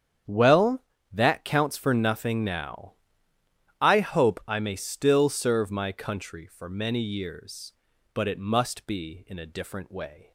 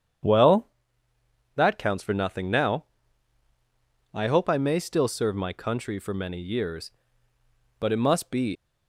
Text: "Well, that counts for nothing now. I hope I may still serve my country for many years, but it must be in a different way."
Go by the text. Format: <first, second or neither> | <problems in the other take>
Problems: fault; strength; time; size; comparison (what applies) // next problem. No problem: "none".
first | starts louder than the rest; strong; until 2.1 s; 8.5 dB; strong in the first // stops before "in a different way"; at 8.5 s